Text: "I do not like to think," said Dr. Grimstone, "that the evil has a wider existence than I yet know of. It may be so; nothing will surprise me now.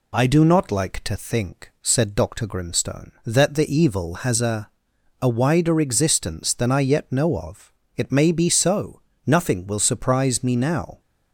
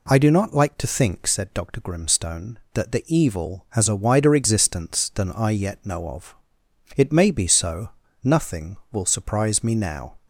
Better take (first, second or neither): second